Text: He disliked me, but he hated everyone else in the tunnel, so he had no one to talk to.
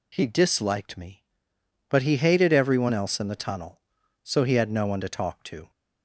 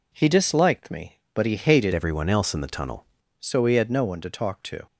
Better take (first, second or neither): first